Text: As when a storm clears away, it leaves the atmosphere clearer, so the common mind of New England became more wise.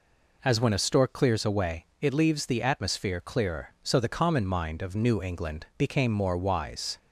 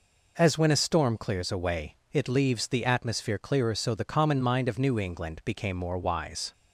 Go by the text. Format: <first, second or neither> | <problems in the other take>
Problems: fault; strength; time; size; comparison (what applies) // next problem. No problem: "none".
second | says "stork" for "storm"; at 0.7 s